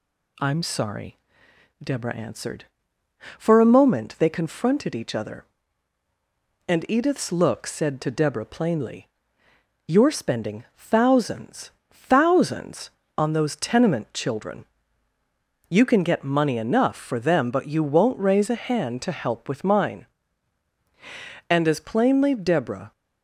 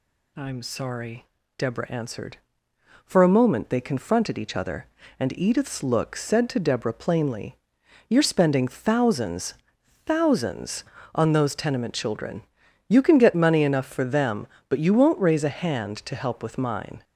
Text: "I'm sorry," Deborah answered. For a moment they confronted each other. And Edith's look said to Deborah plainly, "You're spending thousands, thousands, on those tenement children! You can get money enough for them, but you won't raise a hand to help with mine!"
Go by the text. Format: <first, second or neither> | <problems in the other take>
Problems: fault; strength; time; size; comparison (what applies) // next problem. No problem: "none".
second | goes on to say "And as plainly Deborah"; from 21.4 s on; 1.4 s long